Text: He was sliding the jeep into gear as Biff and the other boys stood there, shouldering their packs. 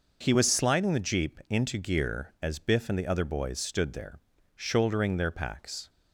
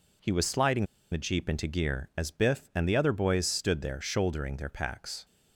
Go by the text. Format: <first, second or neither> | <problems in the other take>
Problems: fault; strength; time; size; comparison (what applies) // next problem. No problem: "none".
first | pauses between "sliding" and "the"; slight; at 0.8 s; 0.26 s long